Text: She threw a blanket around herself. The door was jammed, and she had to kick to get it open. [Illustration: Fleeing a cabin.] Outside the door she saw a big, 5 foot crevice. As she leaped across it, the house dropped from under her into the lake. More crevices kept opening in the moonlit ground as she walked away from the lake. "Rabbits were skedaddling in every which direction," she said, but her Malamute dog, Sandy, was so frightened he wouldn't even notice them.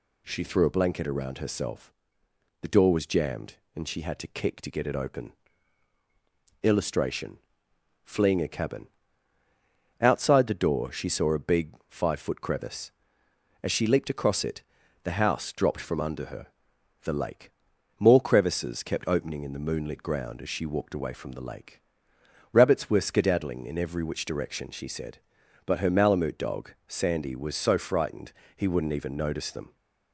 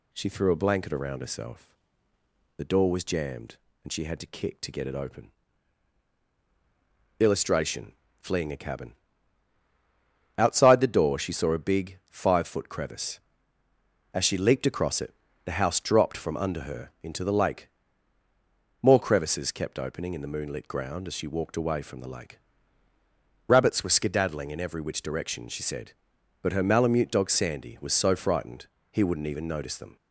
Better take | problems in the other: second | skips "into"; at 16.7 s // pauses between "frightened" and "he"; slight; at 28.3 s; 0.24 s long; slight in the second

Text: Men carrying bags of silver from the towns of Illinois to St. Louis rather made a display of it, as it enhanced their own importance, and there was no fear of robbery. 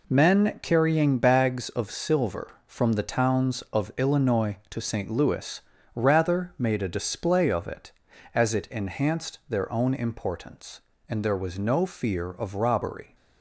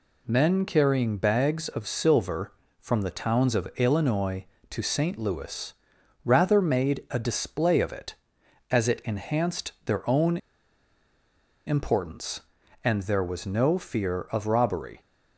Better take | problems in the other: first | pauses between "Louis" and "rather"; noticeable; at 5.7 s; 0.50 s long; slight in the first // pauses between "own" and "importance"; strong; at 10.3 s; 1.2 s long

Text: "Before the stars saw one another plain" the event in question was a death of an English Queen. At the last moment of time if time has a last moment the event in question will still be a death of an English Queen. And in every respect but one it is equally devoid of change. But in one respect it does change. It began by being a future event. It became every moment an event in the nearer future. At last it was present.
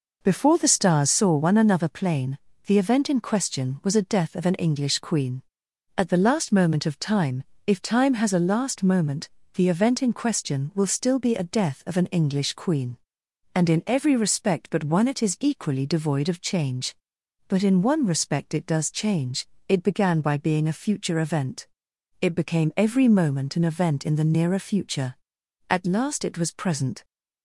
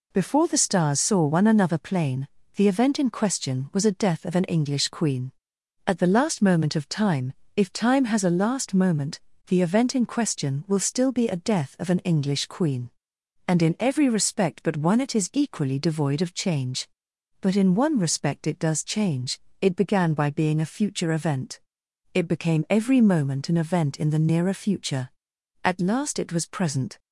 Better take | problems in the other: second | starts louder than the rest; noticeable; until 1.4 s; 5 dB // pauses between "plain" and "the"; slight; at 2.3 s; 0.30 s long; slight in the second // pauses between "time" and "if"; slight; at 7.4 s; 0.22 s long; slight in the second // pauses between "moment" and "the"; slight; at 9.2 s; 0.24 s long; slight in the second

